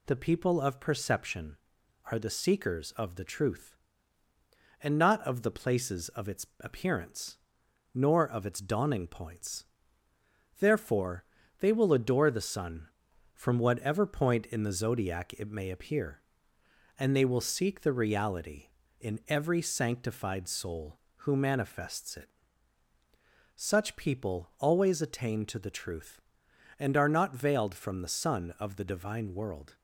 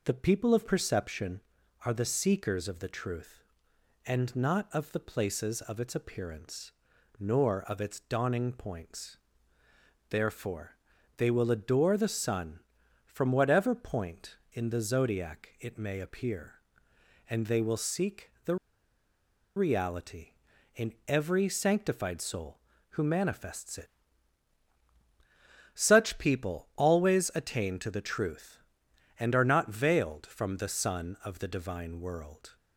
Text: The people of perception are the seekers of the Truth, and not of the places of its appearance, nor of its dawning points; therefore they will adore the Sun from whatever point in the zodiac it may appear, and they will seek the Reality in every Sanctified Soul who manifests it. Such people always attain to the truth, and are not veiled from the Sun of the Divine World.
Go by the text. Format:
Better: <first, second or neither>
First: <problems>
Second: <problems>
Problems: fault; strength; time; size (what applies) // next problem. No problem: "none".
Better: first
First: pauses between "therefore" and "they"; slight; at 11.2 s; 0.34 s long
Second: pauses between "therefore" and "they"; at 10.7 s; 0.40 s long // pauses between "the" and "Reality"; at 18.5 s; 1.0 s long